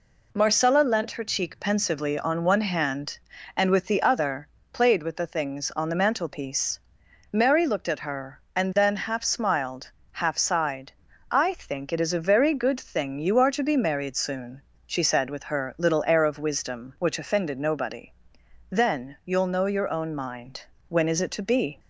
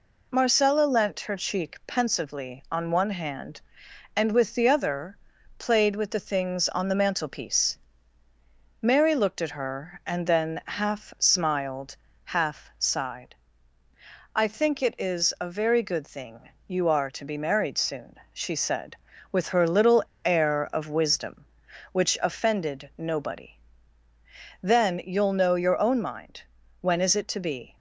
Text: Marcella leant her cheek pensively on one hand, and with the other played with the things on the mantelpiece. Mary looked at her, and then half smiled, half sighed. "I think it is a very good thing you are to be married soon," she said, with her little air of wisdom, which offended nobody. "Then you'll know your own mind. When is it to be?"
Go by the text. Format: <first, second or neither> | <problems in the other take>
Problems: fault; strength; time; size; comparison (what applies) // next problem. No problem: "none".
first | pauses between "other" and "played"; at 5.1 s; 0.44 s long; slight in the first // pauses between "thing" and "you"; slight; at 16.4 s; 0.16 s long // pauses between "little" and "air"; slight; at 20.0 s; 0.20 s long